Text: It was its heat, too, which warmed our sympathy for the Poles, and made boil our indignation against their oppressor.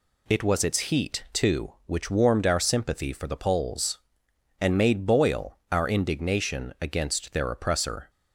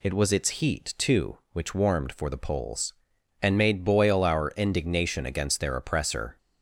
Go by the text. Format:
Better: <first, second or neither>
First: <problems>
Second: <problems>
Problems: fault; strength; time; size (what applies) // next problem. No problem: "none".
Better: first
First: none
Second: skips "our sympathy"; at 2.1 s